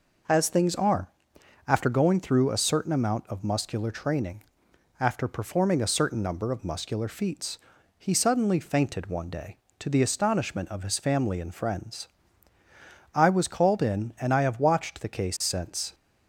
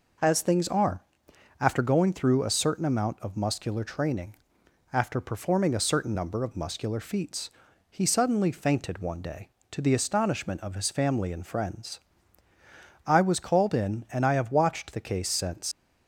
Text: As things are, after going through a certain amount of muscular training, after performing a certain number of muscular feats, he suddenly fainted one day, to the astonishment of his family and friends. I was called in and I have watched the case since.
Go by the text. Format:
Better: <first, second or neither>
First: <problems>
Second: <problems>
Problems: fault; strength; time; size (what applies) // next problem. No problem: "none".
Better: first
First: none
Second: leaves "since" unfinished; at 15.7 s; 115 ms